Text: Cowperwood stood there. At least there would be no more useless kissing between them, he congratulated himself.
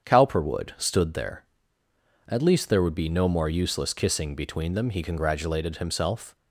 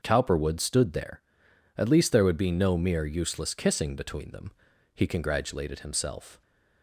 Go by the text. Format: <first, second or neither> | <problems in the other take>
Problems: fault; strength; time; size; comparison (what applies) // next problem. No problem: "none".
first | starts louder than the rest; until 1.0 s; 6.5 dB; strong in the first // says "mere" for "more"; at 2.7 s